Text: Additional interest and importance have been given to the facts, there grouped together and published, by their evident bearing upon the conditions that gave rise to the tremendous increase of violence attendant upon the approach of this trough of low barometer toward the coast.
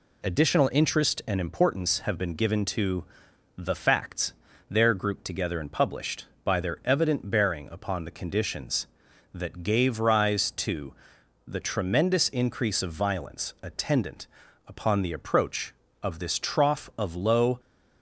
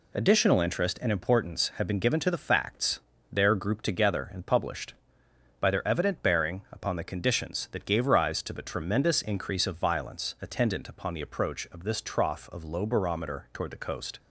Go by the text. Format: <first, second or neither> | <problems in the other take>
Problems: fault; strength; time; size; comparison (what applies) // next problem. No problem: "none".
second | pauses between "to" and "the"; noticeable; at 3.0 s; 0.54 s long // pauses between "to" and "the"; noticeable; at 10.9 s; 0.52 s long // pauses between "attendant" and "upon"; at 14.2 s; 0.40 s long // stops before "barometer toward the coast"; at 17.5 s